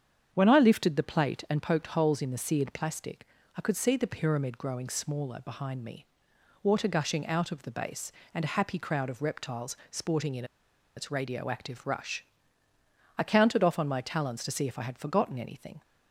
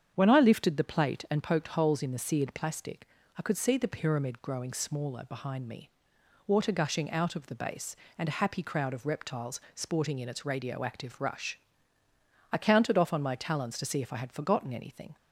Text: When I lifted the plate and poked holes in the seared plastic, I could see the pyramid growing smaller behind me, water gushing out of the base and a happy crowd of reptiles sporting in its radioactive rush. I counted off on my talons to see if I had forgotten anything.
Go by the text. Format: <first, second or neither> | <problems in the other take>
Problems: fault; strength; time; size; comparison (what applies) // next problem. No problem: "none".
second | starts louder than the rest; strong; until 1.3 s; 8 dB; strong in the second // pauses between "in" and "its"; noticeable; at 10.4 s; 0.52 s long